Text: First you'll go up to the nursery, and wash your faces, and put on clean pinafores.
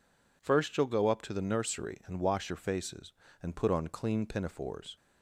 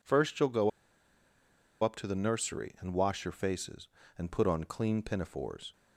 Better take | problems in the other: first | pauses between "go" and "up"; at 0.6 s; 1.1 s long

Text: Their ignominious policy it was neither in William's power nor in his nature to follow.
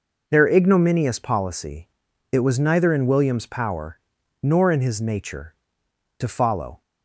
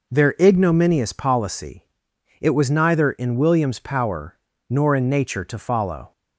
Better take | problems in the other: first | pauses between "policy" and "it"; noticeable; at 1.8 s; 0.58 s long; noticeable in the first // pauses between "power" and "nor"; slight; at 4.3 s; 0.34 s long; also in the first // skips "his"; at 5.0 s

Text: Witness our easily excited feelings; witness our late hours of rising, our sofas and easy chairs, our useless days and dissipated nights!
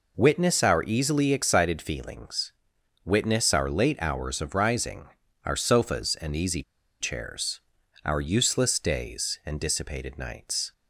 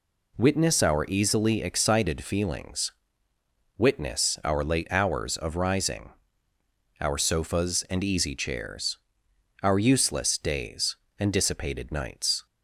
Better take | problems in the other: second | pauses between "easy" and "chairs"; at 6.6 s; 0.38 s long

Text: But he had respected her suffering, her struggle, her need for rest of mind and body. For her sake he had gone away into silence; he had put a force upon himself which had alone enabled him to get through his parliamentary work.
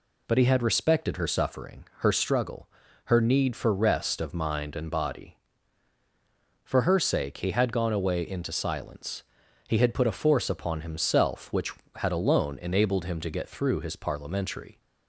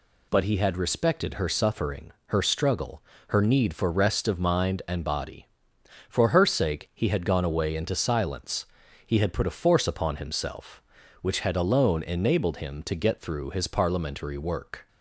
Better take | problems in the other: second | stops before "work"; at 14.7 s

